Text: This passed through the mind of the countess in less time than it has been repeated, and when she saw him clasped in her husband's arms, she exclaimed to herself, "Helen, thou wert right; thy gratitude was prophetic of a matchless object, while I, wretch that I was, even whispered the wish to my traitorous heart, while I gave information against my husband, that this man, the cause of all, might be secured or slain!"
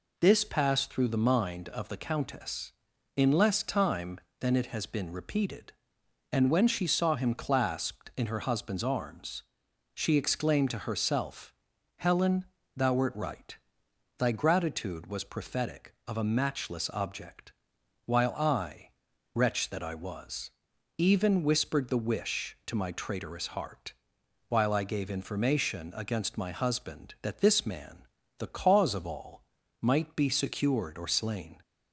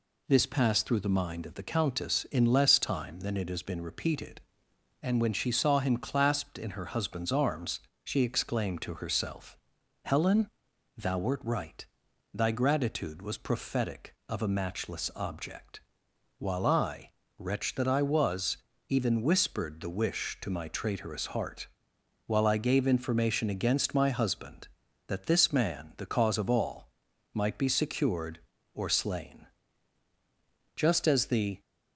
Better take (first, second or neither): first